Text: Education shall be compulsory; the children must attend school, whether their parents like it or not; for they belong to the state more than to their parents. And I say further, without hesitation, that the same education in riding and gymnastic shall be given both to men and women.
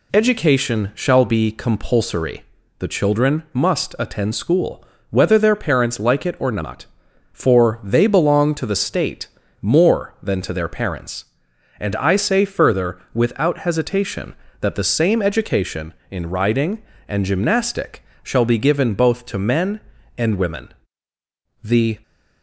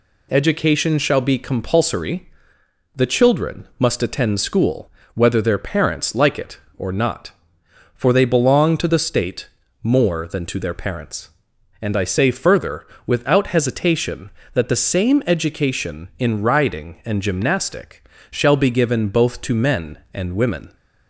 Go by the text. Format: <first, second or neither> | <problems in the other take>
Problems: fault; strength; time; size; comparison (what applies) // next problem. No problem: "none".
second | pauses between "state" and "more"; slight; at 9.2 s; 0.34 s long; slight in the second // pauses between "gymnastic" and "shall"; slight; at 18.0 s; 0.22 s long; slight in the second // goes on to say "The"; slight; from 21.6 s on; 0.38 s long